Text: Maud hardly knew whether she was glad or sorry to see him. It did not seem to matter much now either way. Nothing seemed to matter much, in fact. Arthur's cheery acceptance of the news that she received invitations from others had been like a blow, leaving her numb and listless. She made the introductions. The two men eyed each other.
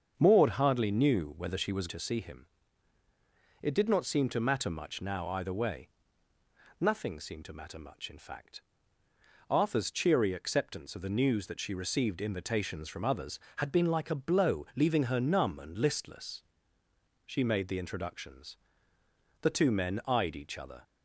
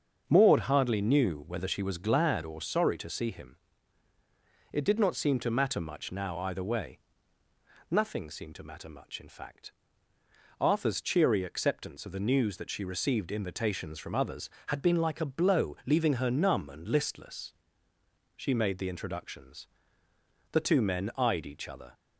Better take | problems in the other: second | starts louder than the rest; until 1.1 s; 7 dB; also in the second // skips "glad or sorry"; at 1.8 s

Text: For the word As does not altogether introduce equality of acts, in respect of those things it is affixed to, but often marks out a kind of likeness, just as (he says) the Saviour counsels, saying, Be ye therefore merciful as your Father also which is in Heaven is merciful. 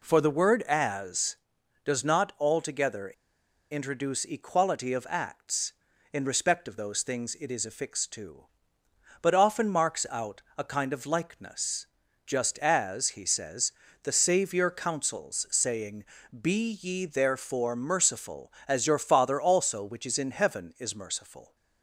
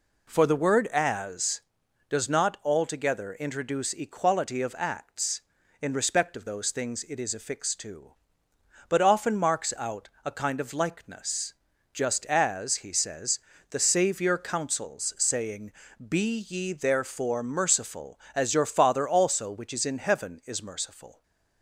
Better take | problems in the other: second | pauses between "altogether" and "introduce"; noticeable; at 3.1 s; 0.60 s long // pauses between "out" and "a"; slight; at 10.4 s; 0.16 s long; slight in the second

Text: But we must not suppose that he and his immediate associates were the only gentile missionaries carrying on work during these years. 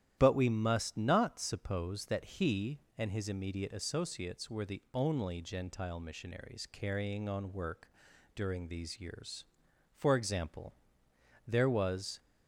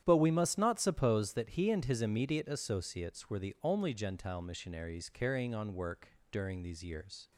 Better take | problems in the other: second | starts louder than the rest; strong; until 1.2 s; 11.5 dB; strong in the second // pauses between "work" and "during"; at 7.8 s; 0.44 s long; slight in the second // goes on to say "For example there was"; strong; from 9.9 s on; 2.2 s long

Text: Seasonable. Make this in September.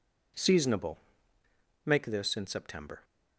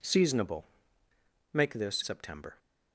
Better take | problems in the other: first | skips "in"; at 2.0 s

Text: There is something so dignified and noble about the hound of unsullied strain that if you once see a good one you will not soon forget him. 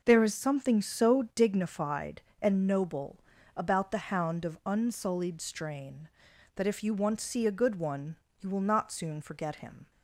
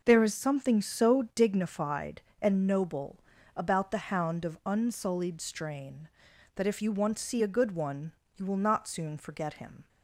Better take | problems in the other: neither | pauses between "noble" and "about"; slight; the same in both // pauses between "one" and "you"; slight; the same in both

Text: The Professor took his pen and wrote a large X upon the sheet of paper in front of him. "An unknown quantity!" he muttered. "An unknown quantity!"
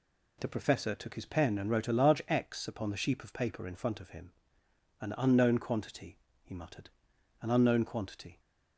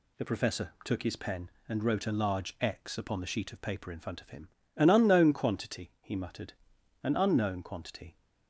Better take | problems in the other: second | says "sheep" for "sheet"; at 2.9 s

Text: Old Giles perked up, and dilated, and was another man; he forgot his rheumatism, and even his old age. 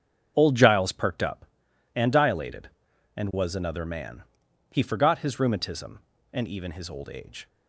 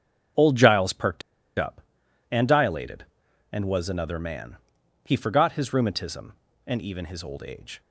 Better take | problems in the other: first | starts louder than the rest; strong; until 1.7 s; 7.5 dB; strong in the first // pauses between "perked" and "up"; at 1.2 s; 0.37 s long

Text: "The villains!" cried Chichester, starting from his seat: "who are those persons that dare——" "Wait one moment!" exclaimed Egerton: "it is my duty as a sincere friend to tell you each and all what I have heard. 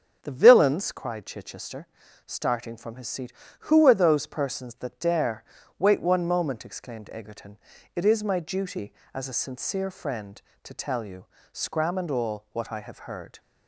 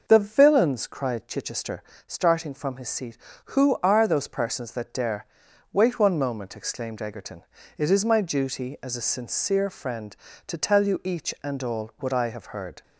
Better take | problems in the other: second | starts louder than the rest; strong; until 1.2 s; 8 dB // says "scram" for "each"; at 11.5 s

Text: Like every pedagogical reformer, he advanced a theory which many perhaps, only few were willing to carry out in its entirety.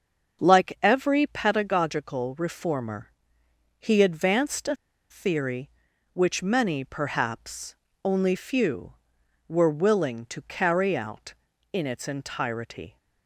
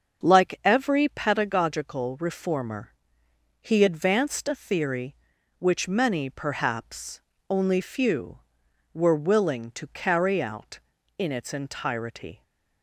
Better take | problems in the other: second | starts louder than the rest; until 1.4 s; 6 dB; also in the second // pauses between "a" and "theory"; slight; at 4.7 s; 0.35 s long

